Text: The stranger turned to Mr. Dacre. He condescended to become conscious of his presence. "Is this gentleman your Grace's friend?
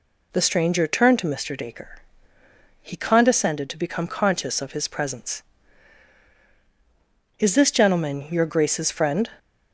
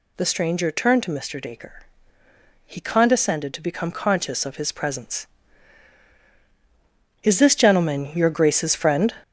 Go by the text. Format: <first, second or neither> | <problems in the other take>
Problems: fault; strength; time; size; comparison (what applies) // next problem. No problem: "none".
first | gets louder; throughout; 6.5 dB